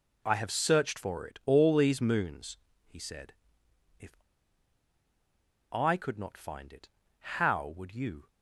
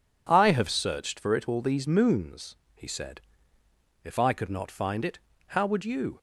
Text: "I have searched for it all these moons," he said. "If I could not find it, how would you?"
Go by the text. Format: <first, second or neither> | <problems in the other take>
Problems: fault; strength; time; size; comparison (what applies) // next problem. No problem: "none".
second | pauses between "If" and "I"; strong; at 4.1 s; 1.5 s long